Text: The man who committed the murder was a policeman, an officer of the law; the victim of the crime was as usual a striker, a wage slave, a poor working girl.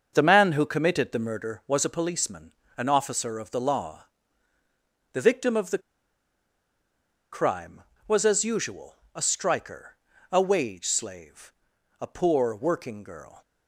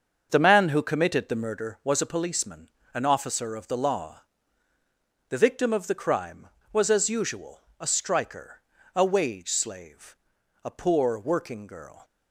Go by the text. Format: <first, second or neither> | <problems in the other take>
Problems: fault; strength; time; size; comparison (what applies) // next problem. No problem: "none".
second | starts louder than the rest; until 1.1 s; 6.5 dB; also in the second // pauses between "the" and "crime"; strong; at 5.8 s; 1.5 s long // pauses between "usual" and "a"; slight; at 8.9 s; 0.18 s long; slight in the second